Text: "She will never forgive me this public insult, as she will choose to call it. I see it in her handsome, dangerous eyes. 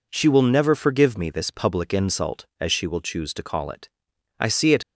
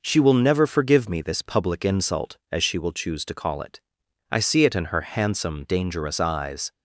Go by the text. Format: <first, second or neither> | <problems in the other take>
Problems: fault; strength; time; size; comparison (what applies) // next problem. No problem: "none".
second | stops before "in her handsome dangerous eyes"; at 4.8 s